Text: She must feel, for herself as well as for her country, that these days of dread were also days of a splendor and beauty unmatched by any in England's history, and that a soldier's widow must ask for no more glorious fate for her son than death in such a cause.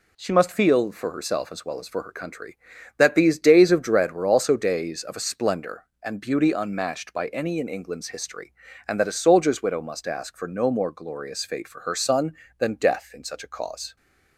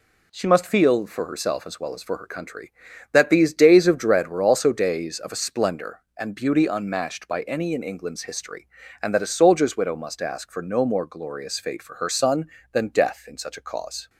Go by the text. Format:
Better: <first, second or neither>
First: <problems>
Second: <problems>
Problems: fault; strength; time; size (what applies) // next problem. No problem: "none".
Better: neither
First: none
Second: none